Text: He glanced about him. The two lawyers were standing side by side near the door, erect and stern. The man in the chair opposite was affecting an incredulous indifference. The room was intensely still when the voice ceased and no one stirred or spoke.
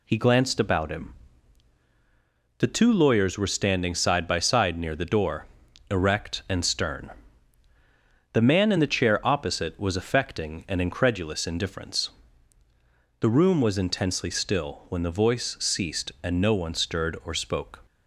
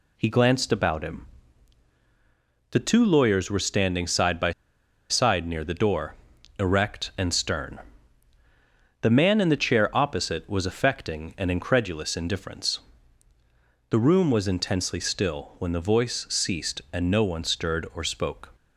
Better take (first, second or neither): first